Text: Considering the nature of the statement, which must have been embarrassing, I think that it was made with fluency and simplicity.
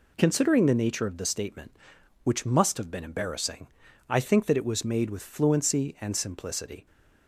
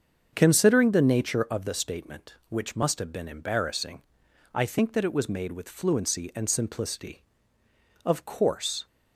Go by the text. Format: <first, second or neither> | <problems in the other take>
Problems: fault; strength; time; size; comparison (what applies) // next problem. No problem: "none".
first | starts louder than the rest; until 1.3 s; 7 dB // goes on to say "Of course"; noticeable; from 8.0 s on; 0.82 s long